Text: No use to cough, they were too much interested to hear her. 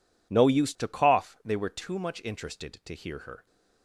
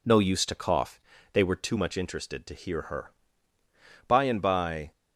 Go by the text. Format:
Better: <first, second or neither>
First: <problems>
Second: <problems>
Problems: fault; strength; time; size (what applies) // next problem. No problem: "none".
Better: first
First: none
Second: goes on to say "By and by"; noticeable; from 4.0 s on; 0.84 s long